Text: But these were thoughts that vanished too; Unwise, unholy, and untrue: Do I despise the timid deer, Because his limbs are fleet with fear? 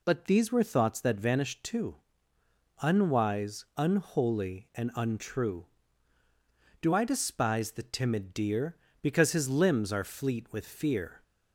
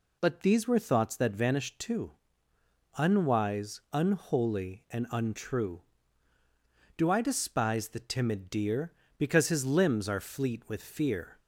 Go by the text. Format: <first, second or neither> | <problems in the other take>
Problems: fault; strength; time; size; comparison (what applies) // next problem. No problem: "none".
neither | none